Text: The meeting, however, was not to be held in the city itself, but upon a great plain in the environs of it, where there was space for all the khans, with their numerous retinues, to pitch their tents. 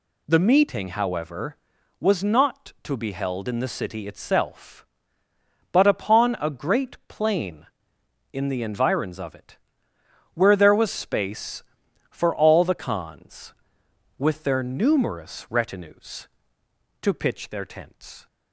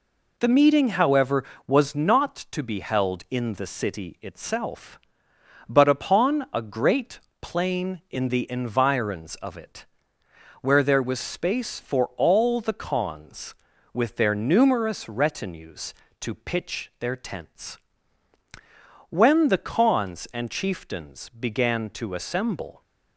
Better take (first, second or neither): first